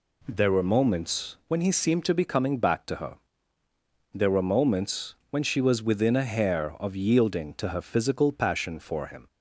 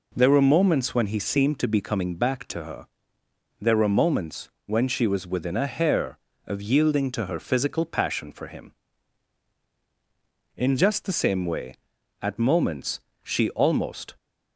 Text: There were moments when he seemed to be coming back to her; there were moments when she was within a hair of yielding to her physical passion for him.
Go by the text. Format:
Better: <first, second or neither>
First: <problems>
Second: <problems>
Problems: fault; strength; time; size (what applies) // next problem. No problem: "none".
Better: first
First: none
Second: pauses between "moments" and "when"; slight; at 4.5 s; 0.16 s long // goes on to say "In just the same way at moments she almost"; strong; from 10.5 s on; 3.5 s long